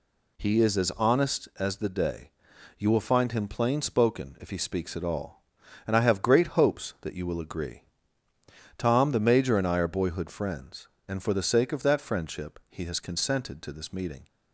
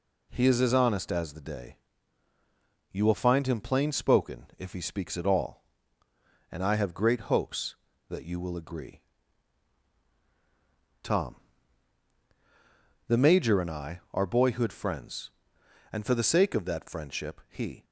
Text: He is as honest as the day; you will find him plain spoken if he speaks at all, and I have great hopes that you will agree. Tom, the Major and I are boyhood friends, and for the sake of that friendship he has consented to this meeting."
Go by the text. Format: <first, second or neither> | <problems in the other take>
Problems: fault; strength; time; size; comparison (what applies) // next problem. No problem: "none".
first | stops before "has consented to this meeting"; at 17.8 s